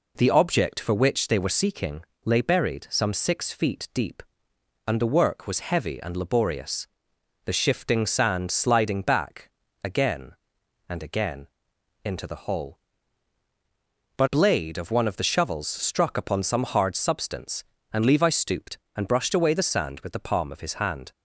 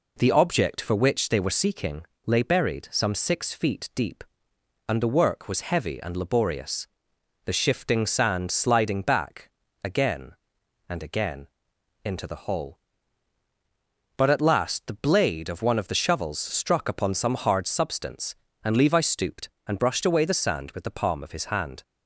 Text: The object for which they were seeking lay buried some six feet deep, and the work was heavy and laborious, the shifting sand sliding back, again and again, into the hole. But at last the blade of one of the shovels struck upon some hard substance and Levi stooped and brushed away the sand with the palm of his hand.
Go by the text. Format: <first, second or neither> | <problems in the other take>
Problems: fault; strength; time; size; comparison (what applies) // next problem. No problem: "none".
second | pauses between "seeking" and "lay"; slight; at 2.0 s; 0.22 s long; slight in the second // skips "at last the"; at 14.2 s